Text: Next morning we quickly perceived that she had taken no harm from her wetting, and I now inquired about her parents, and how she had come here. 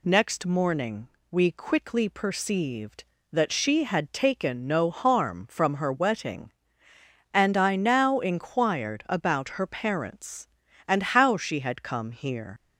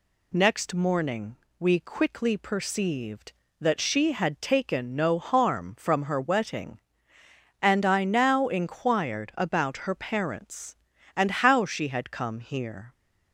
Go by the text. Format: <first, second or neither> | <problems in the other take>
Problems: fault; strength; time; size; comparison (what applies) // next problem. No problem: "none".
second | pauses between "morning" and "we"; slight; at 1.0 s; 0.22 s long; slight in the second // leaves "here" unfinished; at 12.5 s; 100 ms